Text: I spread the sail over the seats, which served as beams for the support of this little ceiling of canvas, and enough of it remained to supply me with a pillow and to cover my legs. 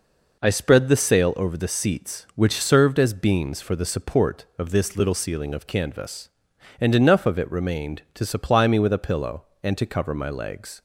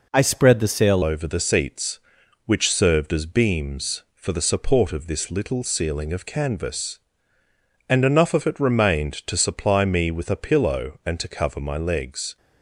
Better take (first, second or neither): first